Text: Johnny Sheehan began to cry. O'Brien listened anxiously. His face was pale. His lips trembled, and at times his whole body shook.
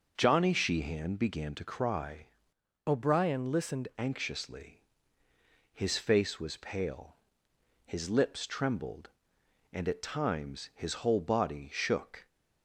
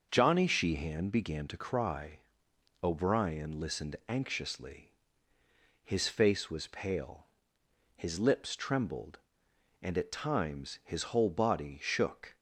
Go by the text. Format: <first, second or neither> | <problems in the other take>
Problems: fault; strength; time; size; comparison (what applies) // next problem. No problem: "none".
second | starts louder than the rest; noticeable; until 1.1 s; 6 dB; also in the second // changes voice from "O'Brien" to "listened"; from 2.8 to 3.8 s; 1.0 s long